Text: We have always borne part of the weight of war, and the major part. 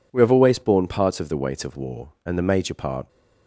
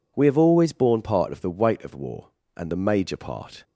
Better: neither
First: none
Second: none

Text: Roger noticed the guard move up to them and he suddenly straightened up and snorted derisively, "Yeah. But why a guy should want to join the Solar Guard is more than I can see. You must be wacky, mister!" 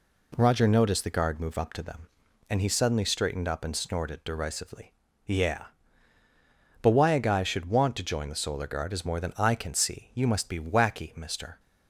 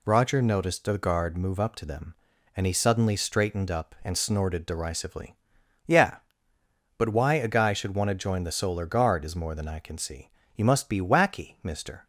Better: neither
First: none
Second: none

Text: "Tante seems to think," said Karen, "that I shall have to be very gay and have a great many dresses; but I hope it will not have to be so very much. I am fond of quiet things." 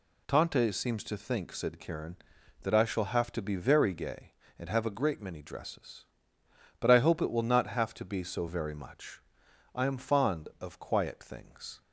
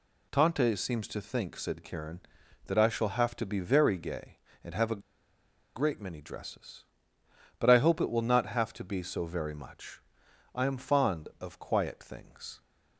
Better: first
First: none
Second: pauses between "a" and "great"; noticeable; at 5.0 s; 0.75 s long

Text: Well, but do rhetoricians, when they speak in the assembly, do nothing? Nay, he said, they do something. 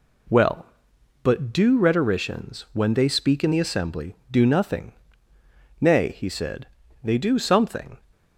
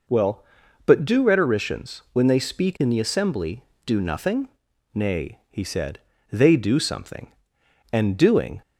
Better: first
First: none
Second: goes on to say "And doing"; noticeable; from 7.9 s on; 0.70 s long

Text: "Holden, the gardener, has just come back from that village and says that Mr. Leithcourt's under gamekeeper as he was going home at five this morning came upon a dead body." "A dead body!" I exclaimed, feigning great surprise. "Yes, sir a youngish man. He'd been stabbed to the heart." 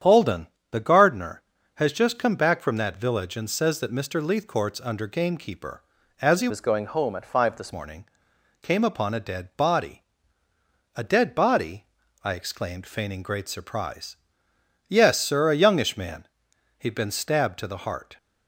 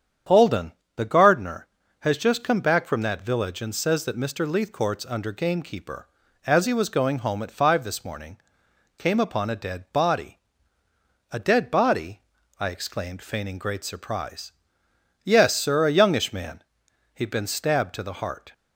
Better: second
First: starts louder than the rest; strong; until 1.2 s; 9 dB // changes voice from "was" to "this"; from 6.4 to 7.7 s; 1.3 s long // pauses between "morning" and "came"; noticeable; at 8.0 s; 0.56 s long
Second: starts louder than the rest; strong; until 1.5 s; 8.5 dB // pauses between "morning" and "came"; noticeable; at 8.3 s; 0.60 s long

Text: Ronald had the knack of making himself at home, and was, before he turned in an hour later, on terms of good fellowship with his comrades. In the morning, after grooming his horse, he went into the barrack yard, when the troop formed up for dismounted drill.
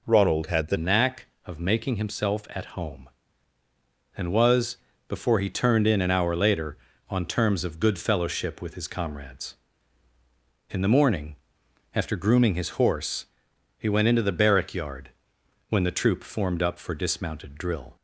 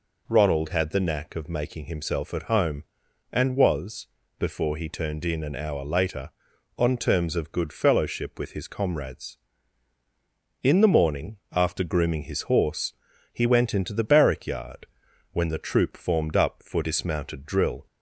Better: second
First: changes voice at "knack"; from 0.7 s on; 17.2 s long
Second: none

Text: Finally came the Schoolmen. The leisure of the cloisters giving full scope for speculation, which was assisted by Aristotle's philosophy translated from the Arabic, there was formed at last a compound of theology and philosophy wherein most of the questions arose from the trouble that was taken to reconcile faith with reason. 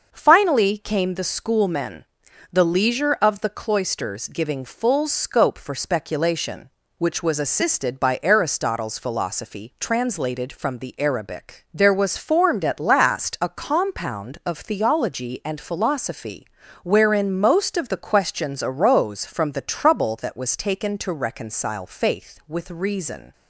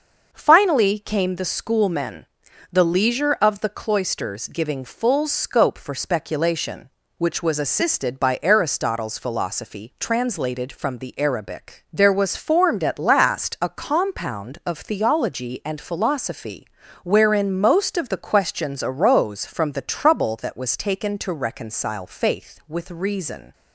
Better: neither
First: starts louder than the rest; noticeable; until 1.1 s; 6 dB // pauses between "philosophy" and "wherein"; slight; at 16.4 s; 0.36 s long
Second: starts louder than the rest; noticeable; until 1.3 s; 6 dB // pauses between "philosophy" and "wherein"; slight; at 16.6 s; 0.36 s long

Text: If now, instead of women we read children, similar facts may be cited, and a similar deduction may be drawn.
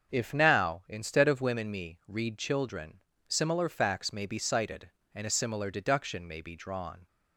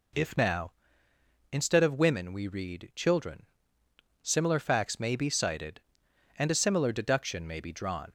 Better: second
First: starts louder than the rest; until 1.1 s; 6.5 dB // says "me" for "we"; at 1.6 s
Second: none

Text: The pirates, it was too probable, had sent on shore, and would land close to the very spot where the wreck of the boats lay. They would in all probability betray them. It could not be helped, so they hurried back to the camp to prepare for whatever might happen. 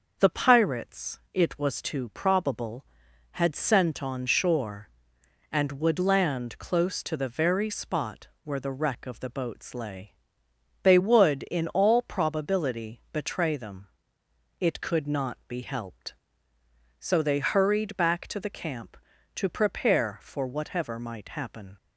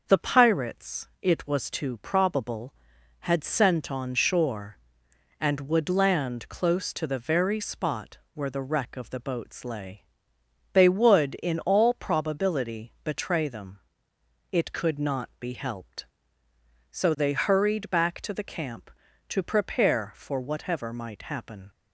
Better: neither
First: starts louder than the rest; until 1.2 s; 6 dB // pauses between "spot" and "where"; slight; at 8.2 s; 0.16 s long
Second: starts louder than the rest; noticeable; until 1.0 s; 6 dB // pauses between "spot" and "where"; slight; at 8.1 s; 0.16 s long

